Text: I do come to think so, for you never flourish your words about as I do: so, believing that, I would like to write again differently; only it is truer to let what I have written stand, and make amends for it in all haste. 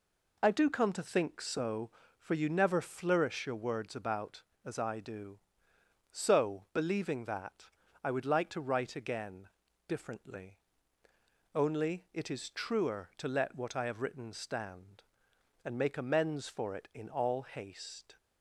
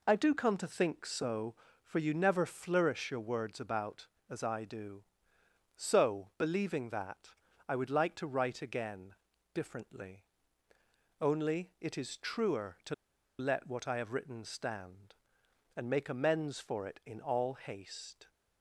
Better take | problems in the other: first | pauses between "again" and "differently"; at 9.1 s; 0.40 s long; also in the first // pauses between "to" and "let"; noticeable; at 12.9 s; 0.45 s long

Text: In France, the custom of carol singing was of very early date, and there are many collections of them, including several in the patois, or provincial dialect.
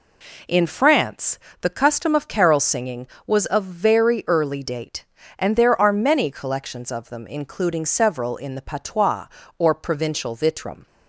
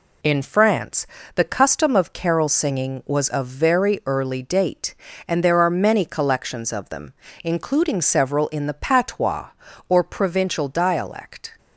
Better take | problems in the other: second | says "vitrum" for "dialect"; at 10.3 s

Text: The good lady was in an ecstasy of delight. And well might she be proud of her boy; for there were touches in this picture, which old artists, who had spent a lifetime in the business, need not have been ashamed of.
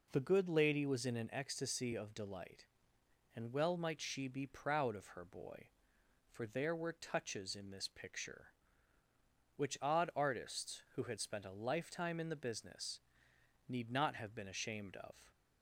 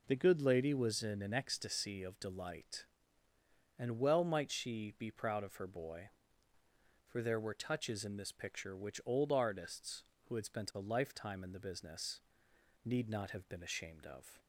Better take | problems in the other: second | says "odd" for "old"; at 9.8 s

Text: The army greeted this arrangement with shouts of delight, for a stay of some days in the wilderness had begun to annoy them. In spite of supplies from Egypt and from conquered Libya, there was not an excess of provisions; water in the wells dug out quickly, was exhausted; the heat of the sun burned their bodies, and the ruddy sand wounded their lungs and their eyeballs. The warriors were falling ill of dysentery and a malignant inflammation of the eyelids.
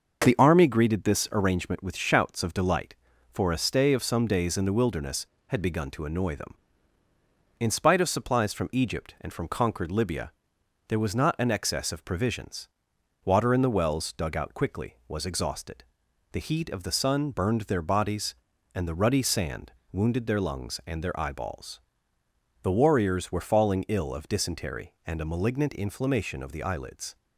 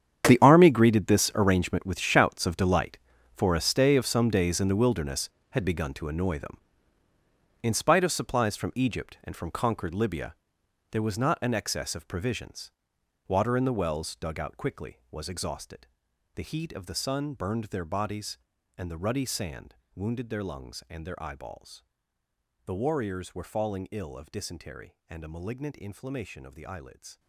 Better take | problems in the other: first | gets quieter; strong; throughout; 16 dB // starts louder than the rest; strong; until 1.3 s; 8.5 dB; noticeable in the first // pauses between "sand" and "wounded"; slight; at 19.7 s; 0.18 s long; slight in the first

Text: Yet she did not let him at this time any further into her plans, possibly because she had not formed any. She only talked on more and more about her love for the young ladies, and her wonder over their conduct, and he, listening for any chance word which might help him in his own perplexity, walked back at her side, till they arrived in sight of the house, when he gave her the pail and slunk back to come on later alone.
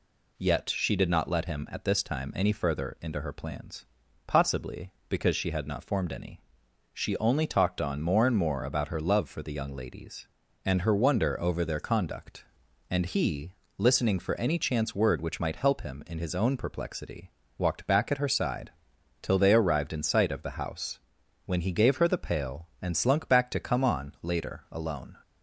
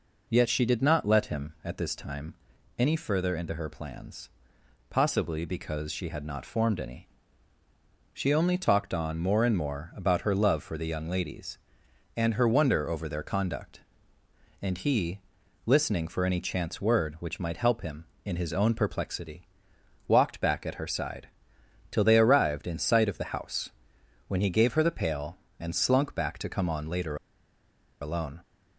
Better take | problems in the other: first | pauses between "time" and "any"; at 2.3 s; 0.44 s long // pauses between "later" and "alone"; noticeable; at 27.1 s; 0.86 s long

